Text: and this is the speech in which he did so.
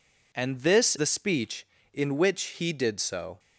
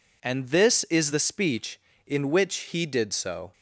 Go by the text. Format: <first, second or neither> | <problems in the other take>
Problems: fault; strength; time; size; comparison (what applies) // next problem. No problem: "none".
second | skips "is"; at 0.9 s